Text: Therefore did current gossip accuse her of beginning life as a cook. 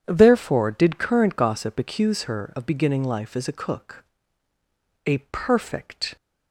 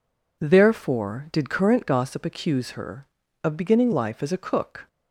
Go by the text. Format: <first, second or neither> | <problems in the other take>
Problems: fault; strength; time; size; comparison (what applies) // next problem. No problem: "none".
second | goes on to say "A perfect"; noticeable; from 5.0 s on; 1.1 s long